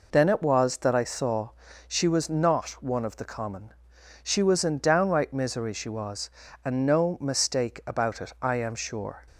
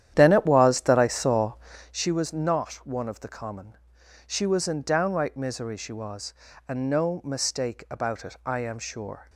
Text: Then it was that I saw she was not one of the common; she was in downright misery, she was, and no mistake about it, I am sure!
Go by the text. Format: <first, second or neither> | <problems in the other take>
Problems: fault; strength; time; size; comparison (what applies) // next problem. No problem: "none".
first | starts louder than the rest; strong; until 2.0 s; 11 dB // pauses between "saw" and "she"; slight; at 1.5 s; 0.36 s long; slight in the first